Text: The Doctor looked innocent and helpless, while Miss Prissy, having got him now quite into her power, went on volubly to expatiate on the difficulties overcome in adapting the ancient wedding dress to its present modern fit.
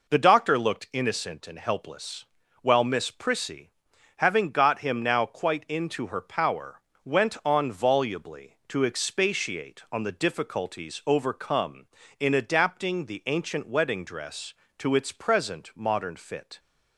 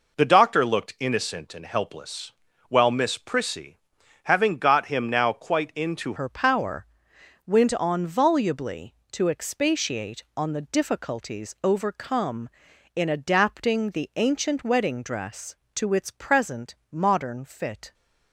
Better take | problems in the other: first | changes voice at "her"; from 6.1 s on; 11.8 s long // pauses between "present" and "modern"; slight; at 16.7 s; 0.16 s long

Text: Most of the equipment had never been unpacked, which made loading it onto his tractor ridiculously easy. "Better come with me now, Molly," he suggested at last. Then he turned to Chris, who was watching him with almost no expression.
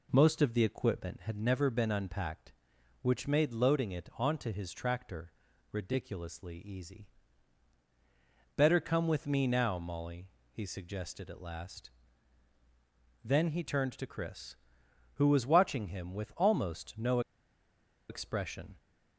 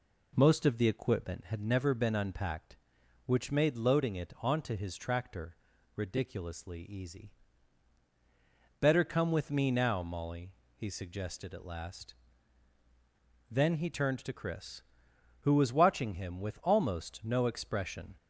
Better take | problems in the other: second | pauses between "tractor" and "ridiculously"; at 5.3 s; 0.38 s long; also in the second // pauses between "no" and "expression"; noticeable; at 17.1 s; 0.89 s long

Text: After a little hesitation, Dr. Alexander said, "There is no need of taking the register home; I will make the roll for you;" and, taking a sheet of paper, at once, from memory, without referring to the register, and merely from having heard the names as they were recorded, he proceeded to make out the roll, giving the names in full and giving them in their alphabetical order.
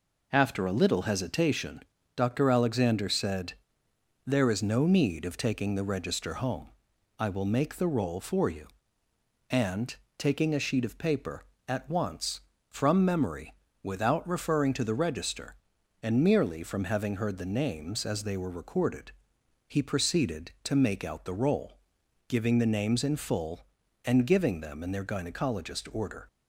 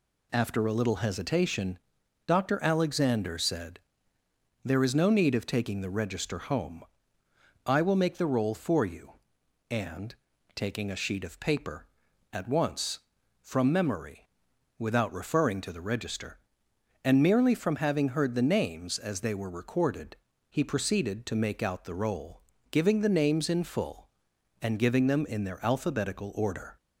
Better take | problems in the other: second | says "gynecologist" for "alphabetical"; at 25.0 s

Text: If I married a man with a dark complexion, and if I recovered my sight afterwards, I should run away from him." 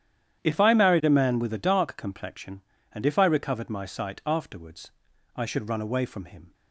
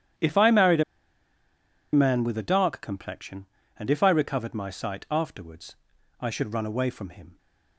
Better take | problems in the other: first | starts louder than the rest; strong; until 2.3 s; 10 dB; strong in the first // pauses between "a" and "man"; at 0.8 s; 1.1 s long

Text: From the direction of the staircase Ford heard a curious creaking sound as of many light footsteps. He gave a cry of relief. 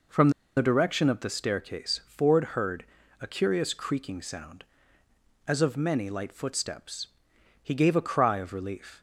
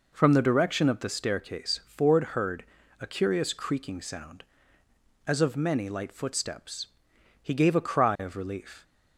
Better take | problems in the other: second | pauses between "From" and "the"; slight; at 0.2 s; 0.26 s long // pauses between "heard" and "a"; slight; at 2.8 s; 0.36 s long; slight in the second

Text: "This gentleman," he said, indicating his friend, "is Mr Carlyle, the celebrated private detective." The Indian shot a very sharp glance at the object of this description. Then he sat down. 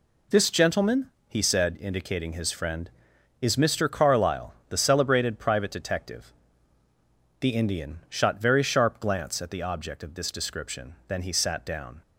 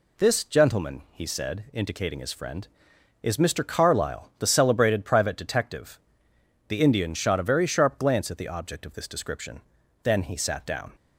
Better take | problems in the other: second | skips "a"; at 8.4 s

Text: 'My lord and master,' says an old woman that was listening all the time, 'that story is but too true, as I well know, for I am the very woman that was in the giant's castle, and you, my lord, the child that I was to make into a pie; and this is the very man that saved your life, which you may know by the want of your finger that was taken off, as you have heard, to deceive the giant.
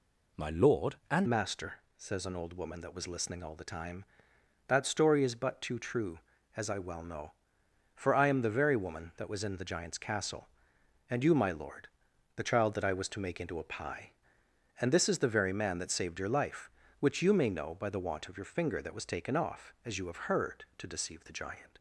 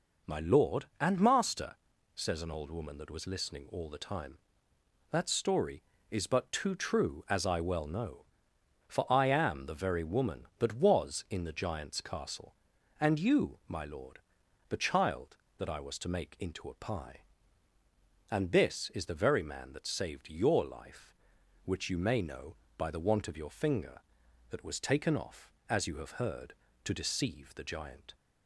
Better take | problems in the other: second | changes voice at "master"; from 1.2 s on; 20.5 s long

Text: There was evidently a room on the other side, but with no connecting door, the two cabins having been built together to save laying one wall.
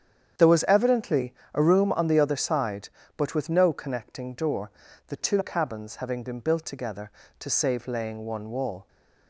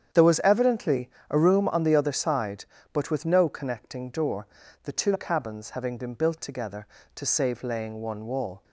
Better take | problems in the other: neither | starts louder than the rest; strong; the same in both // pauses between "evidently" and "a"; slight; the same in both

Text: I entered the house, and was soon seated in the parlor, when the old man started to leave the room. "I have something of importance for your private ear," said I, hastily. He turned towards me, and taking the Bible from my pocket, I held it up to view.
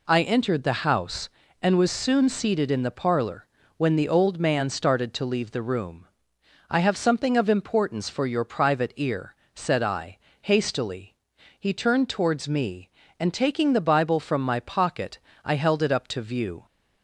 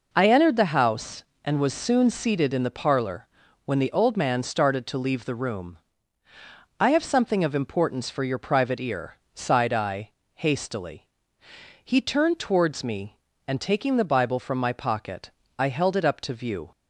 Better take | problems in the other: first | says "sighed" for "said"; at 9.3 s

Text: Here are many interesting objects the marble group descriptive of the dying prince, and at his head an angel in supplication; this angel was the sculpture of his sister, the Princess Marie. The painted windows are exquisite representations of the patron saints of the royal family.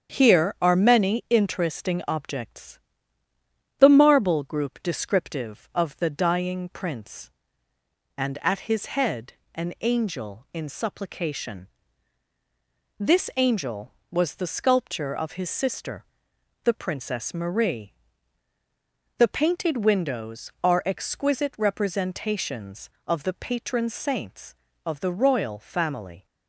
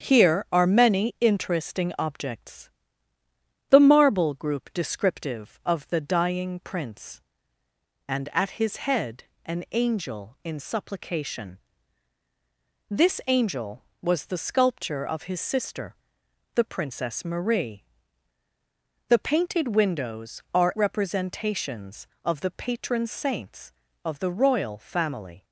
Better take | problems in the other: first | starts louder than the rest; strong; until 1.1 s; 8 dB; strong in the first // pauses between "objects" and "the"; at 2.6 s; 1.0 s long; also in the first // pauses between "head" and "an"; slight; at 9.2 s; 0.20 s long; slight in the first // skips "exquisite"; at 20.7 s

